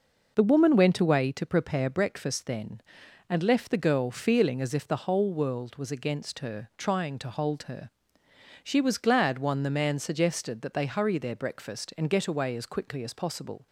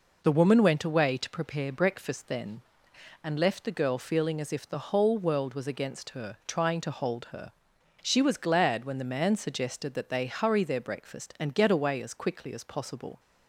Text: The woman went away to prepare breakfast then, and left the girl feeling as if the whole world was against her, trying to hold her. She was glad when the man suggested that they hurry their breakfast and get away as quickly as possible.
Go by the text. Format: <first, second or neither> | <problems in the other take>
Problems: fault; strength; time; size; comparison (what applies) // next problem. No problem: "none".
second | says "one" for "when"; at 9.3 s